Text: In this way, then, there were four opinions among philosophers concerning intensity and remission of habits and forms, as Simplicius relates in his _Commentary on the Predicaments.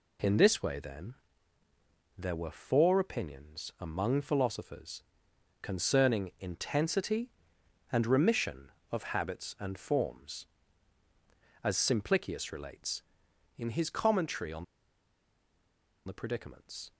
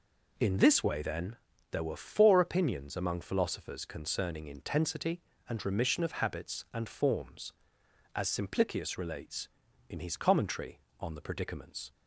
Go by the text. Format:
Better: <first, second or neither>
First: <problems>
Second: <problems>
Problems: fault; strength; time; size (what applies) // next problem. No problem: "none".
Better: second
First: pauses between "philosophers" and "concerning"; noticeable; at 5.0 s; 0.60 s long // pauses between "on" and "the"; strong; at 14.6 s; 1.4 s long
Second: none